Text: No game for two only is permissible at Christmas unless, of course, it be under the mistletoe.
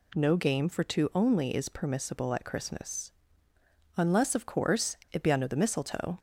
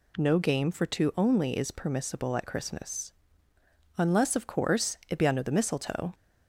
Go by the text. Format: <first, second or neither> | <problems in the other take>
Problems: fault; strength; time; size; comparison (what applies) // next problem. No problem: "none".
neither | pauses between "Christmas" and "unless"; noticeable; the same in both